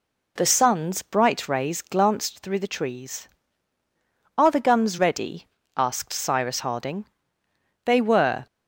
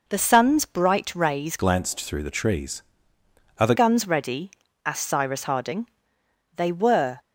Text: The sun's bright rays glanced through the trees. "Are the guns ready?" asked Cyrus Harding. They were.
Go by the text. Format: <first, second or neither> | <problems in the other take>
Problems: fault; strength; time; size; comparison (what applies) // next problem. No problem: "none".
first | changes voice from "glanced" to "the"; from 1.5 to 3.7 s; 2.2 s long